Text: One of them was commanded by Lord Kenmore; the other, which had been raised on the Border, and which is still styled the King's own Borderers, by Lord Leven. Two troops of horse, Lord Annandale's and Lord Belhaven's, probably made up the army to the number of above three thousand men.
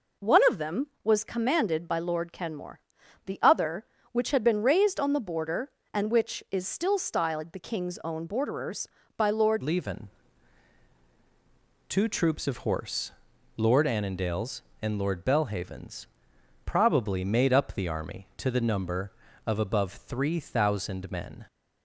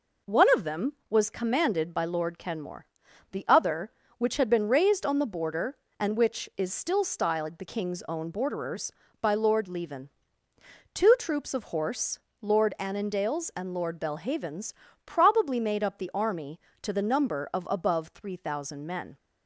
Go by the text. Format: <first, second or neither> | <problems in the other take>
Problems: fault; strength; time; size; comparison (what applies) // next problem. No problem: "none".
second | changes voice at "Leven"; from 9.6 s on; 11.8 s long